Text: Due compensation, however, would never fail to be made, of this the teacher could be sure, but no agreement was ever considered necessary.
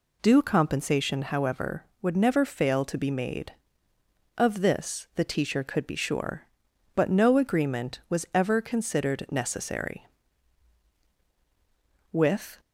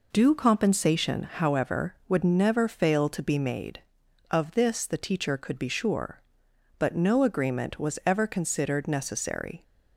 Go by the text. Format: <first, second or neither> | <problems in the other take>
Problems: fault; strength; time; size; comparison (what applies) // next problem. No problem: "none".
second | goes on to say "With"; slight; from 12.1 s on; 0.48 s long